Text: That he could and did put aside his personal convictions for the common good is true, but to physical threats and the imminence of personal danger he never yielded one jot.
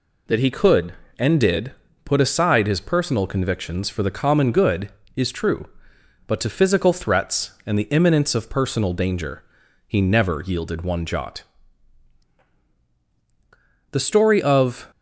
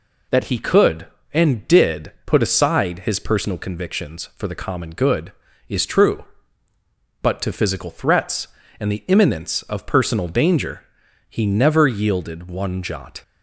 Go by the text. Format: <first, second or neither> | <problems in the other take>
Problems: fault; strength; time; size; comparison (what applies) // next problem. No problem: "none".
second | pauses between "did" and "put"; slight; at 1.7 s; 0.32 s long // pauses between "danger" and "he"; at 9.4 s; 0.44 s long; noticeable in the second // goes on to say "The story of"; noticeable; from 13.9 s on; 0.98 s long